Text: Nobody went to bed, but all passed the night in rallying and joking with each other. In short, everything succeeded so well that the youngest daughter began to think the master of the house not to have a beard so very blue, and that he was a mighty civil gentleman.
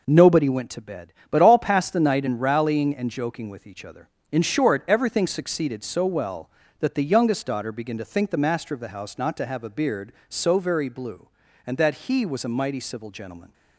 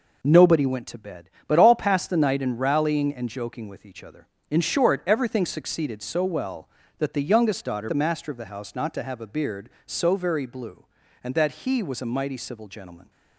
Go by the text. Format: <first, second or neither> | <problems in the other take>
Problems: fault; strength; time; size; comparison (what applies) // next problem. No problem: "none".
first | skips "began to think"; at 7.8 s